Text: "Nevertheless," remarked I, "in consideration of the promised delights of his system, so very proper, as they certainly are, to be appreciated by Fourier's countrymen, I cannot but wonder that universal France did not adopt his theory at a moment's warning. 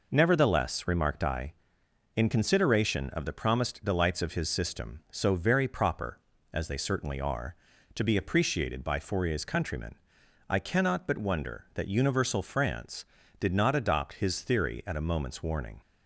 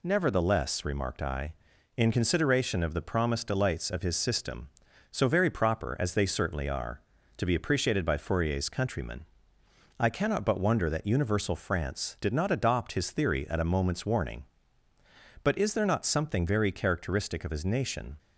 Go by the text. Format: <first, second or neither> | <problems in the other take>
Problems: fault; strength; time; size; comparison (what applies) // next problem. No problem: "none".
first | goes on to say "But is there not something very characteristic of his nation"; strong; from 15.4 s on; 2.7 s long